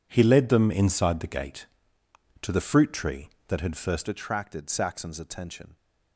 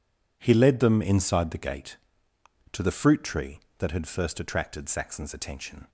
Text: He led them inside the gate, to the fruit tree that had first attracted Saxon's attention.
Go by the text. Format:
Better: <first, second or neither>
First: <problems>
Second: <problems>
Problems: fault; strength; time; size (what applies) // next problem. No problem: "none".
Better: second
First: changes voice at "attracted"; from 4.0 s on; 1.7 s long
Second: none